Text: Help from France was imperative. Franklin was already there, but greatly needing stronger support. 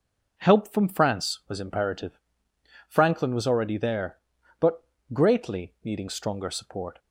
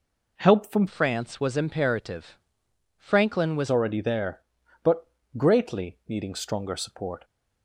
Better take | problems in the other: first | changes voice from "France" to "was"; from 0.8 to 3.7 s; 2.9 s long // pauses between "but" and "greatly"; slight; at 5.0 s; 0.30 s long; slight in the first

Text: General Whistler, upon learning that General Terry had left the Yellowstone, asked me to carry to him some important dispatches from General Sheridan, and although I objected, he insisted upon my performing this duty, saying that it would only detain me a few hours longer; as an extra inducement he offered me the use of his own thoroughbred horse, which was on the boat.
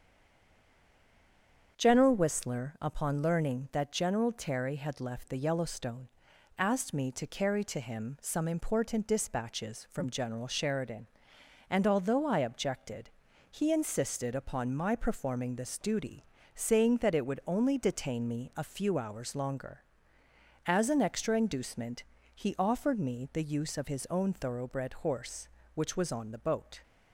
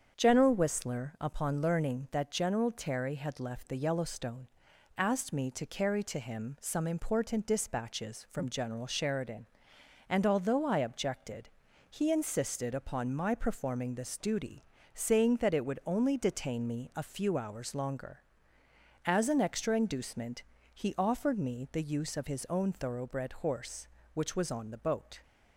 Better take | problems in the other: second | stays silent before the first word; noticeable; until 1.7 s; 1.7 s long // starts louder than the rest; strong; until 2.8 s; 7.5 dB; strong in the second // pauses between "inducement" and "he"; slight; at 22.0 s; 0.28 s long; slight in the second

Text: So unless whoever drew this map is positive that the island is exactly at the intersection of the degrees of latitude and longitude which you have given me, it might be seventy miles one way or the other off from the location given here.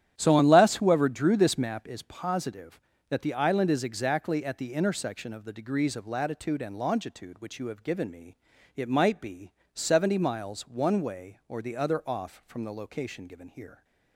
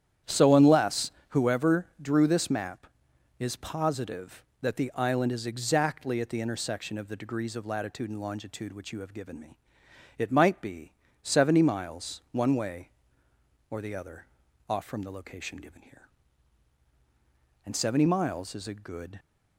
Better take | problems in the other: first | starts louder than the rest; strong; until 1.4 s; 10 dB; strong in the first // pauses between "unless" and "whoever"; slight; at 1.0 s; 0.20 s long // pauses between "be" and "seventy"; slight; at 10.9 s; 0.30 s long; slight in the first // pauses between "other" and "off"; at 14.2 s; 0.42 s long // goes on to say "And seventy miles is a good"; from 17.6 s on; 1.5 s long

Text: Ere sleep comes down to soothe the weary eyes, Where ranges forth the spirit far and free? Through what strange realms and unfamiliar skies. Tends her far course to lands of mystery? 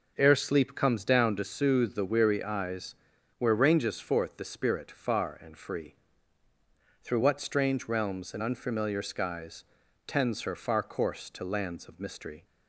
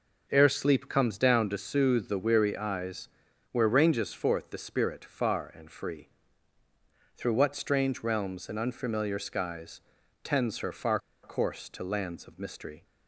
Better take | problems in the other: first | pauses between "far" and "course"; slight; at 10.9 s; 0.24 s long

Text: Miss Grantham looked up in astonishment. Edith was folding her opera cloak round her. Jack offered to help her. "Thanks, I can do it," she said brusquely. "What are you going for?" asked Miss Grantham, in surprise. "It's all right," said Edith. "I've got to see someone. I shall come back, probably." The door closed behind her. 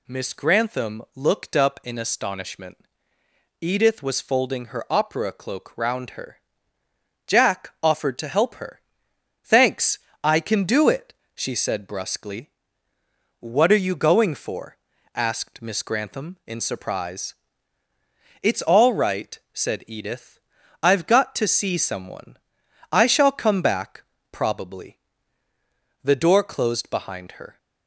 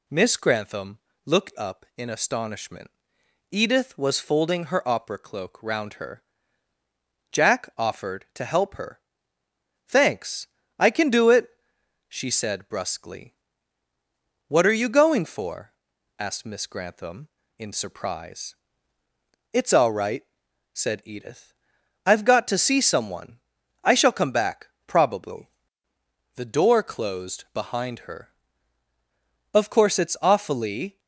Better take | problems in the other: first | pauses between "Grantham" and "looked"; slight; at 0.9 s; 0.26 s long // goes on to say "Of course it's awfully"; from 29.5 s on; 1.4 s long

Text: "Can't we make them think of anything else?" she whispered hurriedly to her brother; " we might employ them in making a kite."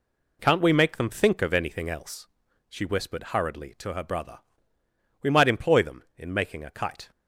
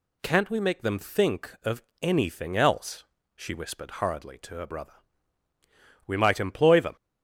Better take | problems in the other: first | pauses between "of" and "anything"; slight; at 1.8 s; 0.20 s long // stops before "in making a kite"; at 6.9 s

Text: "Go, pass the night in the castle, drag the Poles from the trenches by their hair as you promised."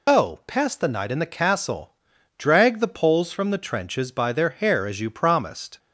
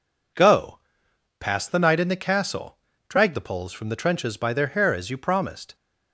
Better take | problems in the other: second | loses the start of "Go"; at 0.0 s; 90 ms

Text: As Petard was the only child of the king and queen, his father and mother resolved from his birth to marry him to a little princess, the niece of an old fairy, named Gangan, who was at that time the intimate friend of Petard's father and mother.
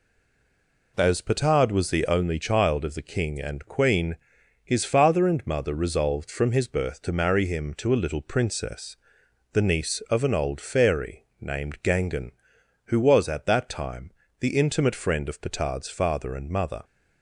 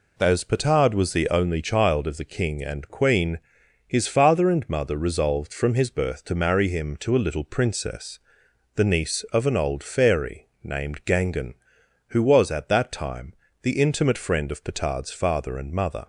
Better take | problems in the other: second | stays silent before the first word; slight; until 0.9 s; 0.9 s long // pauses between "time" and "the"; slight; at 14.1 s; 0.28 s long; slight in the second

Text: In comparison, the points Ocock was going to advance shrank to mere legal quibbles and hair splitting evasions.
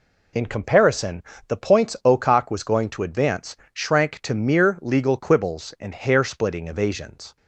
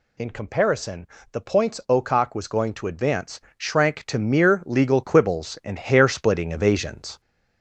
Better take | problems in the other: first | gets louder; slight; throughout; 3 dB // pauses between "advance" and "shrank"; slight; at 3.3 s; 0.18 s long; slight in the first

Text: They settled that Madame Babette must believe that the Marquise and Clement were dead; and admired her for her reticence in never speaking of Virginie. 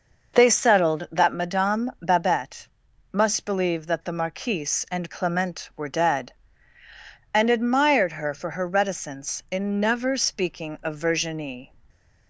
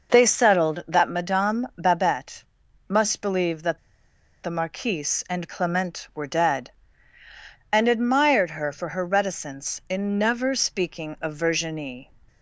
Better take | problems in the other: first | pauses between "Babette" and "must"; noticeable; at 2.4 s; 0.46 s long; noticeable in the first // pauses between "that" and "the"; noticeable; at 3.7 s; 0.64 s long

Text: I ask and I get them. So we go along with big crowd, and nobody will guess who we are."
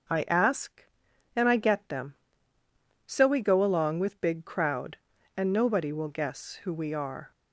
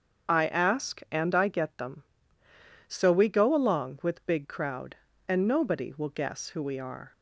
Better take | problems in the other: first | loses the start of "I"; at 0.2 s; 40 ms // starts louder than the rest; strong; until 1.3 s; 7 dB

